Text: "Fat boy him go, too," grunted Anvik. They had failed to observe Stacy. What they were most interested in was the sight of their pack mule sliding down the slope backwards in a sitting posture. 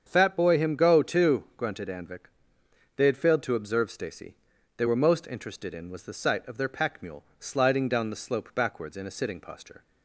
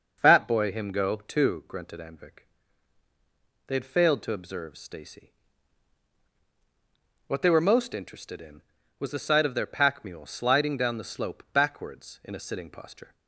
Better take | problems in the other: second | starts louder than the rest; strong; until 1.0 s; 7.5 dB // skips "What"; at 4.5 s // pauses between "mule" and "sliding"; slight; at 7.2 s; 0.16 s long

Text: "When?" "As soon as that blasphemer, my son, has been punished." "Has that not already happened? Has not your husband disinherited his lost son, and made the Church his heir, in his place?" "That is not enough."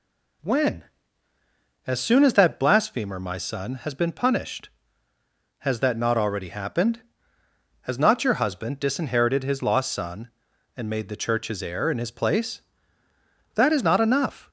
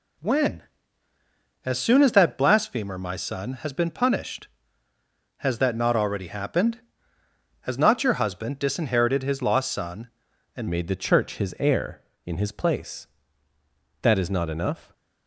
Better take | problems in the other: first | changes voice at "made"; from 10.6 s on; 4.3 s long

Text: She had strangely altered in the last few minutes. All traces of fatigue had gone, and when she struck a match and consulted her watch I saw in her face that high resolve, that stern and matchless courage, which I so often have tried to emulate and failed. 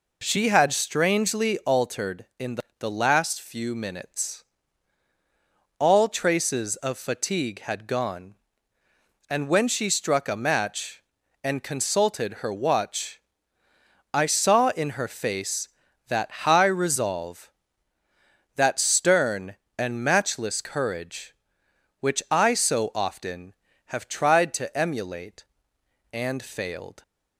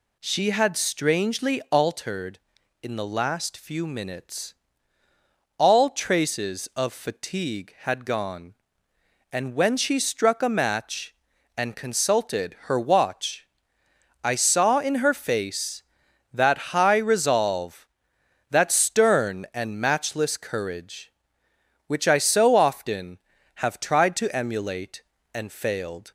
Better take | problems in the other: second | says "the" twice; at 2.7 s // pauses between "watch" and "I"; noticeable; at 13.2 s; 0.94 s long; noticeable in the second // pauses between "that" and "high"; slight; at 16.3 s; 0.16 s long; slight in the second

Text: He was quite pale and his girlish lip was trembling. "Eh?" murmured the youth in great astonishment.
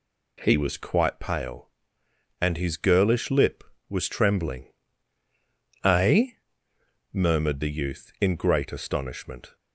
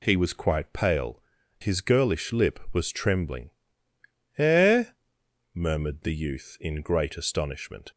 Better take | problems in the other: first | skips "and"; at 1.4 s

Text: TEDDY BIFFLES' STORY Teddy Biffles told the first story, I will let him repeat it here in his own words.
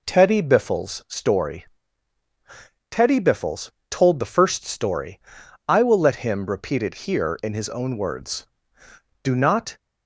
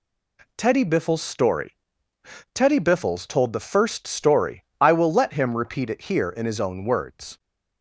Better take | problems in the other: second | pauses between "STORY" and "Teddy"; at 1.6 s; 1.2 s long; noticeable in the second // pauses between "Biffles" and "told"; slight; at 3.7 s; 0.18 s long // goes on to say "Do not"; from 9.2 s on; 0.56 s long

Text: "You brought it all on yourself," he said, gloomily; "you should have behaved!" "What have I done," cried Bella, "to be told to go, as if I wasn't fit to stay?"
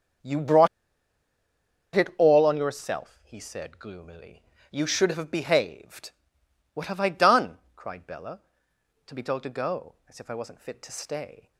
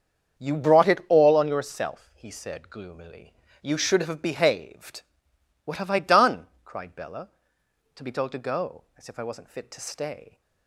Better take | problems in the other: second | starts louder than the rest; strong; until 2.5 s; 7.5 dB; strong in the second // pauses between "brought" and "it"; strong; at 0.6 s; 1.2 s long

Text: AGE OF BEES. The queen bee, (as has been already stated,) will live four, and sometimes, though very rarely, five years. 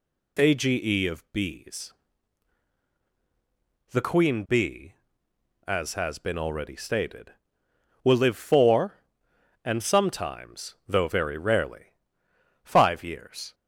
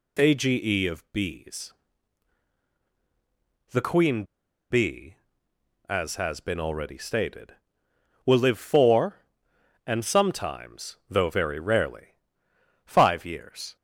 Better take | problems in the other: first | pauses between "queen" and "bee"; noticeable; at 4.2 s; 0.46 s long

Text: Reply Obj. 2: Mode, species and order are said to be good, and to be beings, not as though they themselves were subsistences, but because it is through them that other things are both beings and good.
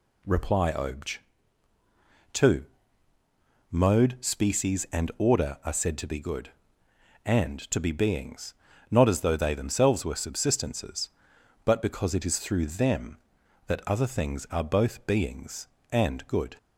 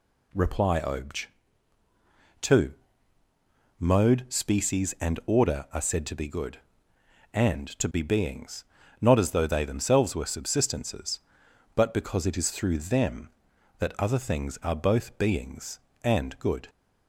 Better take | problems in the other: neither | none

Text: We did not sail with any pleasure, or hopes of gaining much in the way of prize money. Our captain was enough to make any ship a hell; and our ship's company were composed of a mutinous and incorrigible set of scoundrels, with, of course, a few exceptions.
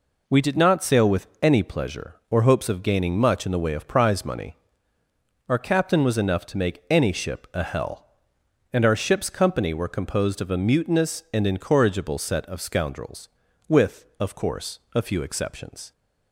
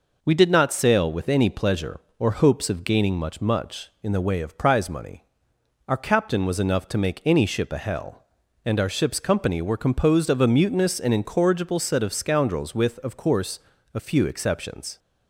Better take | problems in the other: first | says "much" twice; at 3.4 s

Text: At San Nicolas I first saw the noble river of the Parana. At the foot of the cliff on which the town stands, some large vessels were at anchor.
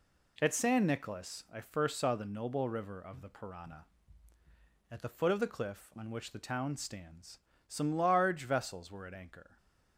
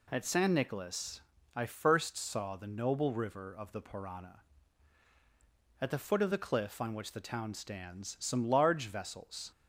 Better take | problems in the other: first | pauses between "Nicolas" and "I"; slight; at 1.2 s; 0.34 s long // stops before "were at anchor"; at 9.5 s

